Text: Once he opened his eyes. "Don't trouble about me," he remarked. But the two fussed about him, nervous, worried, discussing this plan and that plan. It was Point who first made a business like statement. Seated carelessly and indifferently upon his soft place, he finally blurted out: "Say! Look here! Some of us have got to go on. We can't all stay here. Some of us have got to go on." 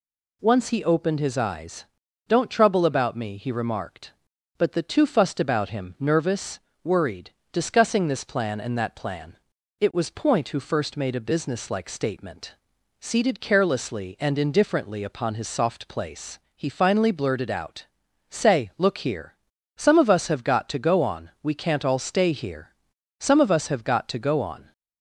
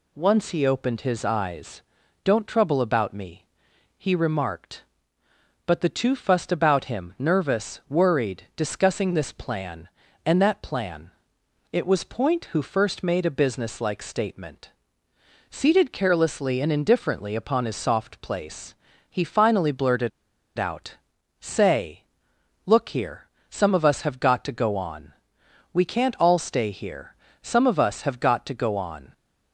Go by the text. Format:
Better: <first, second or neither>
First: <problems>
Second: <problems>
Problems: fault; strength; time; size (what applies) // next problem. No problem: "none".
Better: first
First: none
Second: pauses between "blurted" and "out"; noticeable; at 20.1 s; 0.48 s long